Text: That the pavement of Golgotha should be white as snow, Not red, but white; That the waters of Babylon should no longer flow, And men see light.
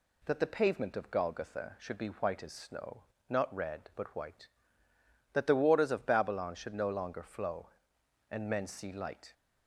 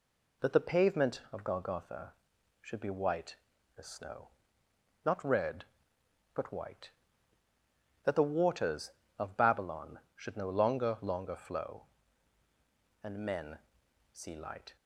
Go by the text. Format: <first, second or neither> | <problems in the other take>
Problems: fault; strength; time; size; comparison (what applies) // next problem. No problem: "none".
first | says "longer" twice; at 11.0 s // pauses between "men" and "see"; noticeable; at 13.5 s; 0.56 s long